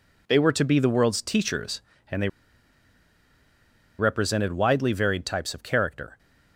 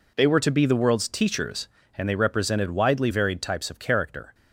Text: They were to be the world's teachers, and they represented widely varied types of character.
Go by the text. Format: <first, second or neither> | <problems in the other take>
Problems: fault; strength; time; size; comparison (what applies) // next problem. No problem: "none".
second | pauses between "they" and "represented"; strong; at 2.2 s; 1.6 s long